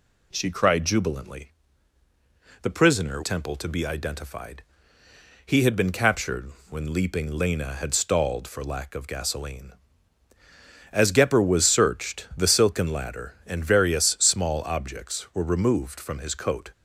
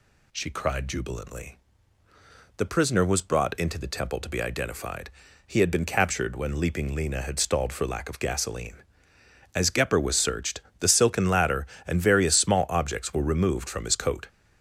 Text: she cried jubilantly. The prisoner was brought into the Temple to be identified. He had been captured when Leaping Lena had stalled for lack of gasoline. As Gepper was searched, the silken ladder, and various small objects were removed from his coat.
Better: second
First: skips "was brought into the"; at 3.2 s // pauses between "captured" and "when"; slight; at 6.5 s; 0.18 s long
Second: none

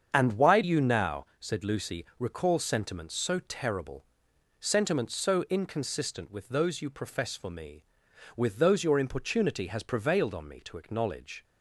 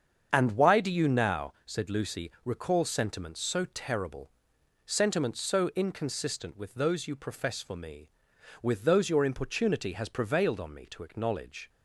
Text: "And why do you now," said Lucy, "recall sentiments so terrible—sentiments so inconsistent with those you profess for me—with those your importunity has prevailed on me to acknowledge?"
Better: second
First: starts louder than the rest; strong; until 1.1 s; 7.5 dB // skips "do"; at 0.6 s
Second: starts louder than the rest; strong; until 1.3 s; 7 dB

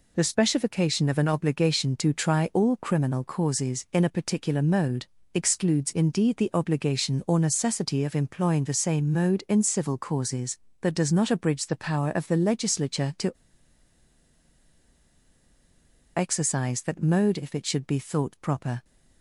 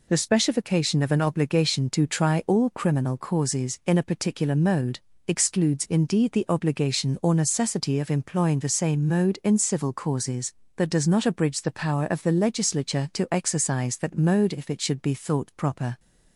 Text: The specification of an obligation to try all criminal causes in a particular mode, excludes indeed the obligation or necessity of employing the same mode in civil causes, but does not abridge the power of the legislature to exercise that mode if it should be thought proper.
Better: second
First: pauses between "to" and "exercise"; strong; at 13.3 s; 2.8 s long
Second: none

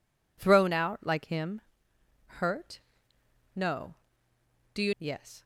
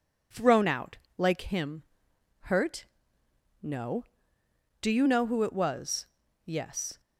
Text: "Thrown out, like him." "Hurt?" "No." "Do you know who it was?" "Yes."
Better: second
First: skips "know who it was"; at 4.9 s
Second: none

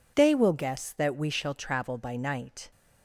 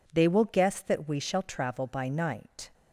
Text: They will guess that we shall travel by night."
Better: neither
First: none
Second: none

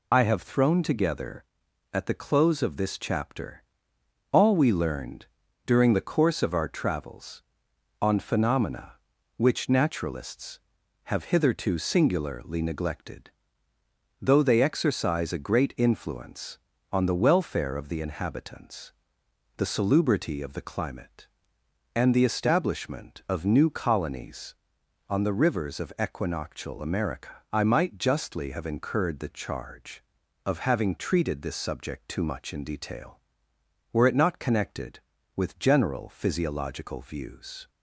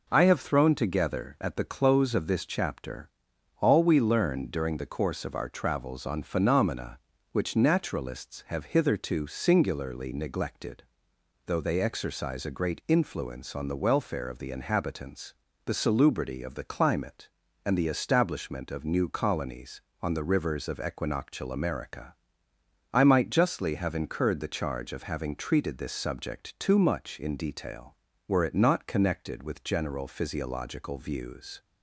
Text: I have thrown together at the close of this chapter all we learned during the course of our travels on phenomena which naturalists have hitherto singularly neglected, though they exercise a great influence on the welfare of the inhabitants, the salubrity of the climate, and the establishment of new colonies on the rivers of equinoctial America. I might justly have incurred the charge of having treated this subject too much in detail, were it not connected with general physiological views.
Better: second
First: loses the start of "I"; at 0.1 s; 50 ms // pauses between "chapter" and "all"; noticeable; at 3.6 s; 0.68 s long // pauses between "learned" and "during"; at 5.2 s; 0.40 s long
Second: pauses between "chapter" and "all"; noticeable; at 3.0 s; 0.50 s long

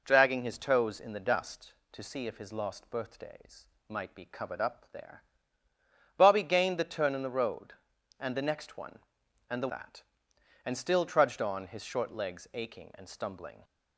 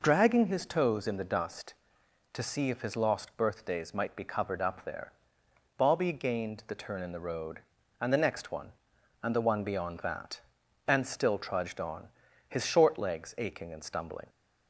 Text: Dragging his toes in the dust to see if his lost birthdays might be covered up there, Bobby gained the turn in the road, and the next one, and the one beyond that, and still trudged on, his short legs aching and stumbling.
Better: second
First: pauses between "birthdays" and "might"; slight; at 3.6 s; 0.20 s long // skips "one beyond"; at 9.6 s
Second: none

